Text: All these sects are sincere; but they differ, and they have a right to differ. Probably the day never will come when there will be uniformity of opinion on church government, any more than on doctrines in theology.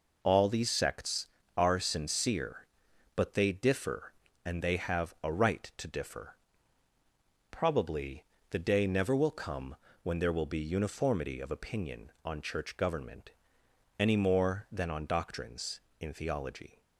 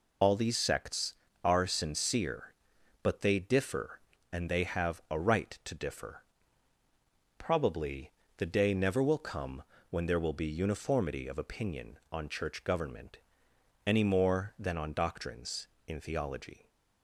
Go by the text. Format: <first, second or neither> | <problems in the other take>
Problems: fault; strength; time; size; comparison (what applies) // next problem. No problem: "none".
first | loses the start of "All"; at 0.2 s; 110 ms // pauses between "Probably" and "the"; slight; at 8.1 s; 0.24 s long; slight in the first // pauses between "come" and "when"; slight; at 9.6 s; 0.26 s long; slight in the first